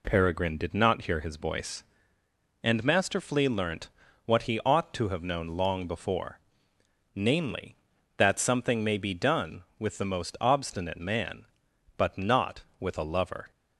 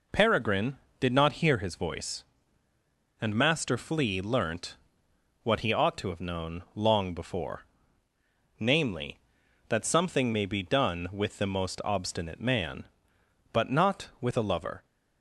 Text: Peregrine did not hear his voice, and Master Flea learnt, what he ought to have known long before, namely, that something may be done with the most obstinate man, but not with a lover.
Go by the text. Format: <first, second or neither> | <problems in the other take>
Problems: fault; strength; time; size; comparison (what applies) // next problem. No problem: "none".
neither | none